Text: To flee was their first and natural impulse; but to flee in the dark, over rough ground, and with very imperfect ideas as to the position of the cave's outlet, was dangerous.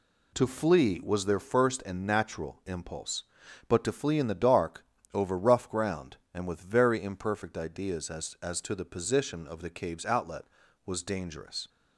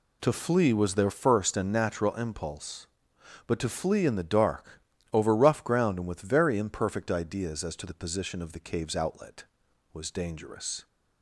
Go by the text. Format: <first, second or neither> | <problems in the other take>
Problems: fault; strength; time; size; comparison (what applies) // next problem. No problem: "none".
second | says "as" twice; at 8.4 s